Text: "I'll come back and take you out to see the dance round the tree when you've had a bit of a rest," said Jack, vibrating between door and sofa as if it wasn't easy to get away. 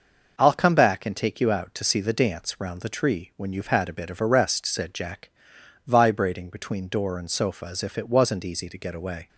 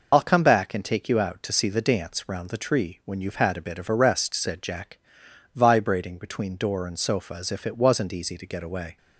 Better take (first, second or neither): first